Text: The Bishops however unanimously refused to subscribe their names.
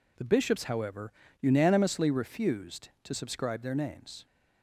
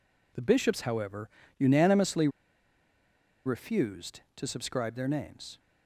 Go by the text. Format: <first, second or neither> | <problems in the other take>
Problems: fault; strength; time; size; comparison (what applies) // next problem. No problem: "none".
first | pauses between "however" and "unanimously"; slight; at 1.2 s; 0.30 s long; slight in the first // pauses between "unanimously" and "refused"; at 2.2 s; 1.1 s long